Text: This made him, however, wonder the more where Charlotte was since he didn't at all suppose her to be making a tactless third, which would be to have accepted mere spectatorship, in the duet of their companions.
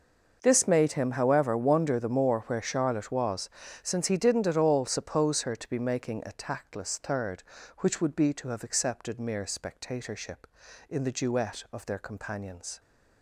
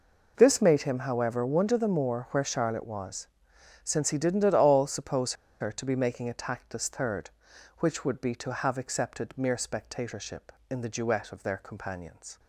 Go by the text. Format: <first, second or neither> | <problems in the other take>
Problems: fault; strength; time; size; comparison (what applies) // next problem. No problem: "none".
first | pauses between "was" and "since"; noticeable; at 3.2 s; 0.58 s long; slight in the first // pauses between "suppose" and "her"; slight; at 5.3 s; 0.26 s long